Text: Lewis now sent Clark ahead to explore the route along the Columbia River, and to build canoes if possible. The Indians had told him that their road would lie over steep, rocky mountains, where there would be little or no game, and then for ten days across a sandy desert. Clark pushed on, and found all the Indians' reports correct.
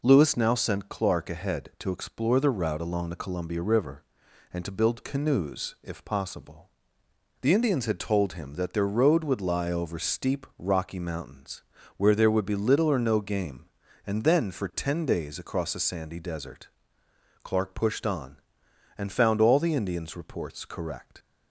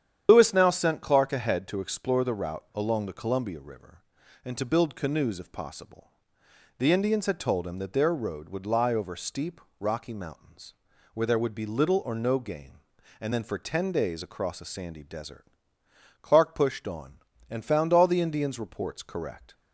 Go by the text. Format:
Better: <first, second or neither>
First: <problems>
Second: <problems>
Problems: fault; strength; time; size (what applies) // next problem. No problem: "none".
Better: first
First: none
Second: loses the start of "Lewis"; at 0.2 s; 120 ms // starts louder than the rest; strong; until 1.3 s; 9.5 dB